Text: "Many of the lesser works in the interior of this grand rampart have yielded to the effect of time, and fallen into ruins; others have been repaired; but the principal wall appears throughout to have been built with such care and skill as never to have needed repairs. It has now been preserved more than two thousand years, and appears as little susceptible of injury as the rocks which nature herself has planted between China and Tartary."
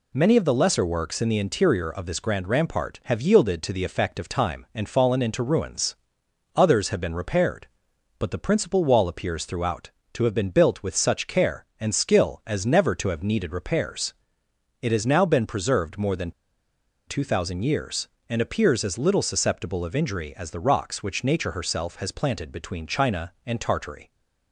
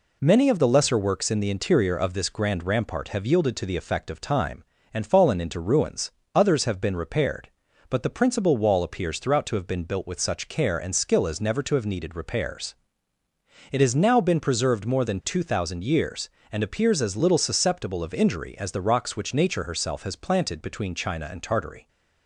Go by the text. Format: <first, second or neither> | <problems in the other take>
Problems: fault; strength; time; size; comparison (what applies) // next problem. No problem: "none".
second | pauses between "than" and "two"; noticeable; at 16.3 s; 0.76 s long